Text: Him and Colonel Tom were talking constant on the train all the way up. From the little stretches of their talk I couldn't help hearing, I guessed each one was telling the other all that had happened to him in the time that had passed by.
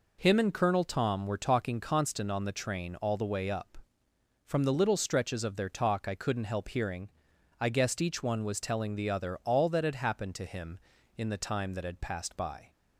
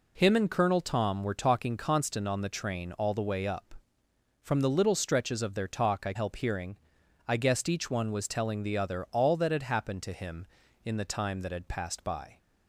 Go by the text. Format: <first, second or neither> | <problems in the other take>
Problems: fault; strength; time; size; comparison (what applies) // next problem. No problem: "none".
first | skips "couldn't"; at 6.1 s